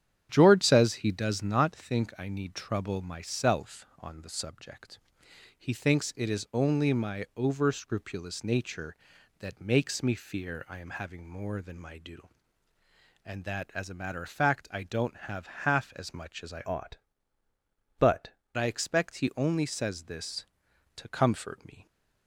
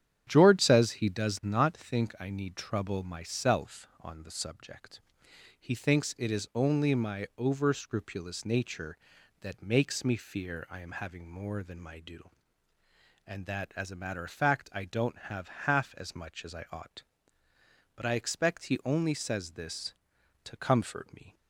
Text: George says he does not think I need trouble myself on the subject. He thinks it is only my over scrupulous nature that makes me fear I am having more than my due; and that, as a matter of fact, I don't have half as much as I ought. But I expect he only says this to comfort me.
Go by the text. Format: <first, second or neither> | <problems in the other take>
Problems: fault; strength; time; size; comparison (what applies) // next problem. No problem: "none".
second | starts louder than the rest; strong; until 1.3 s; 9.5 dB; strong in the second // pauses between "have" and "half"; slight; at 15.4 s; 0.18 s long; slight in the second // changes voice from "ought" to "But"; from 16.6 to 18.3 s; 1.7 s long